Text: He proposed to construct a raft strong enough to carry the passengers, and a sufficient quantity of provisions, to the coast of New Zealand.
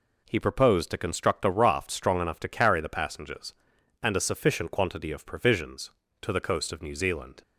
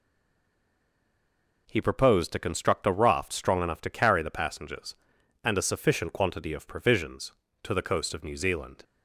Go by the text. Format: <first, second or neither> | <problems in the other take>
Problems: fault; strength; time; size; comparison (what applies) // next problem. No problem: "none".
first | stays silent before the first word; noticeable; until 1.6 s; 1.6 s long